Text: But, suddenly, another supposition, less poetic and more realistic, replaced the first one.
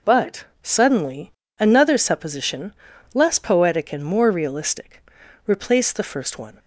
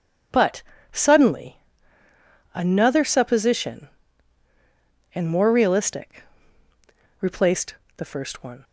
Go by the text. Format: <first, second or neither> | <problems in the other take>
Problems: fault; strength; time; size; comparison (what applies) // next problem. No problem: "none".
first | skips "less poetic"; at 4.5 s // pauses between "replaced" and "the"; slight; at 7.7 s; 0.24 s long